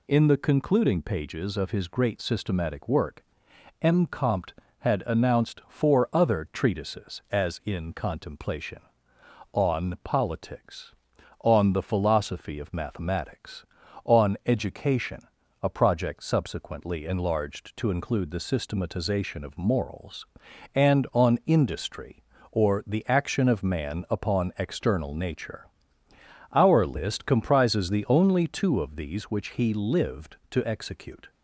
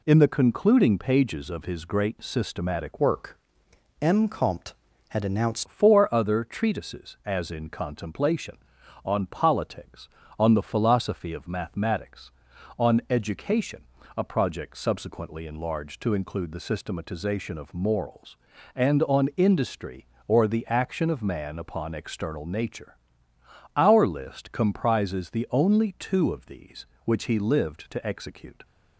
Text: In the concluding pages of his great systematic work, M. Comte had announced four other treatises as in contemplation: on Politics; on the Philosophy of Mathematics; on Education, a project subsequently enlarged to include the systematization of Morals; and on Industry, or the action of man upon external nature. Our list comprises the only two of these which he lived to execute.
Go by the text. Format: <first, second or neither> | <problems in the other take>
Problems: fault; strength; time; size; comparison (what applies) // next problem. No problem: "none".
first | changes voice from "work" to "announced"; from 2.9 to 5.6 s; 2.7 s long